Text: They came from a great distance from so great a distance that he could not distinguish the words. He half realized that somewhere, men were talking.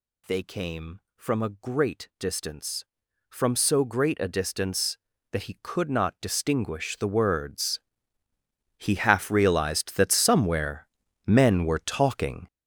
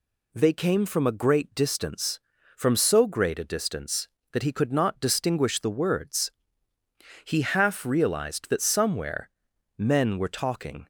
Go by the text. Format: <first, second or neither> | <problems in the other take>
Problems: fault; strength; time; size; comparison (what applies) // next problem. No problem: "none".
second | gets louder; strong; throughout; 9.5 dB